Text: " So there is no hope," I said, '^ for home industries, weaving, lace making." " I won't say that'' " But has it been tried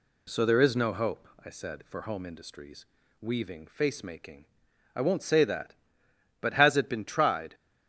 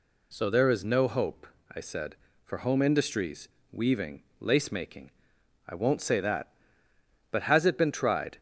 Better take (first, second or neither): second